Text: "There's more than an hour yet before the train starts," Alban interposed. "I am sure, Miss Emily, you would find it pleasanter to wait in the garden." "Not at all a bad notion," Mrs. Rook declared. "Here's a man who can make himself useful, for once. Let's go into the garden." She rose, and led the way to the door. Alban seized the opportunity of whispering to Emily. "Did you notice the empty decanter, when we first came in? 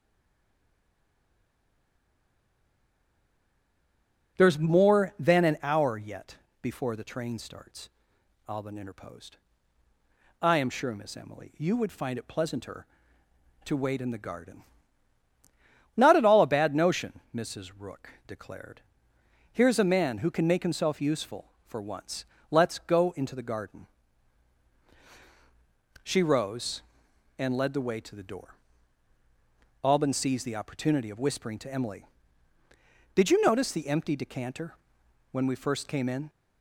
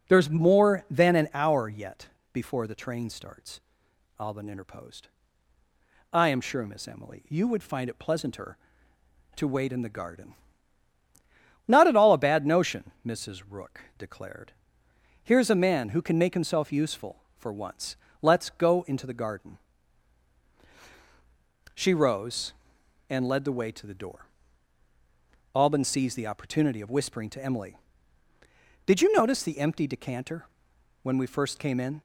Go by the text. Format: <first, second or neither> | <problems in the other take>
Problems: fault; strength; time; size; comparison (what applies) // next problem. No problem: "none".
second | stays silent before the first word; strong; until 4.3 s; 4.3 s long // pauses between "yet" and "before"; slight; at 6.3 s; 0.24 s long; slight in the second // pauses between "Rook" and "declared"; slight; at 18.0 s; 0.16 s long; slight in the second